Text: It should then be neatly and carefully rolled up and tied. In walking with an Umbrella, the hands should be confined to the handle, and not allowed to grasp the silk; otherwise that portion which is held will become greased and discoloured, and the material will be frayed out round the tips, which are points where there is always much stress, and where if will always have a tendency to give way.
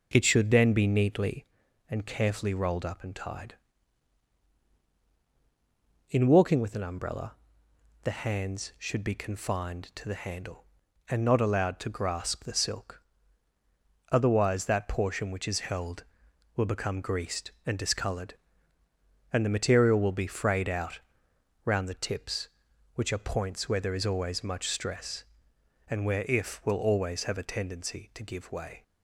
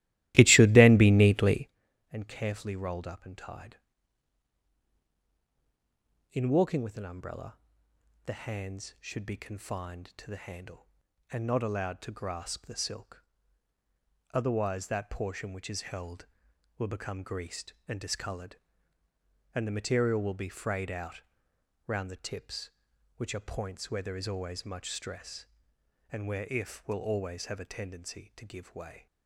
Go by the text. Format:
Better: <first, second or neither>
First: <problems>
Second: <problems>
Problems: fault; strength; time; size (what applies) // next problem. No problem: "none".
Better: first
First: pauses between "out" and "round"; noticeable; at 21.0 s; 0.64 s long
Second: starts louder than the rest; strong; until 1.8 s; 16 dB // pauses between "out" and "round"; noticeable; at 21.2 s; 0.64 s long